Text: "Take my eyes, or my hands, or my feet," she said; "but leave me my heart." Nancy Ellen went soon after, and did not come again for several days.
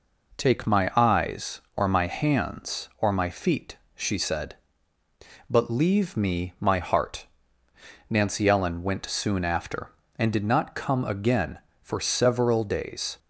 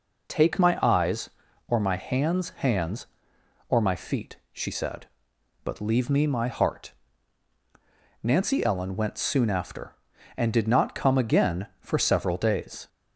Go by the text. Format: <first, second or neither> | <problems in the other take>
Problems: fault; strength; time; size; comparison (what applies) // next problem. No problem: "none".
first | says "hands" twice; at 2.4 s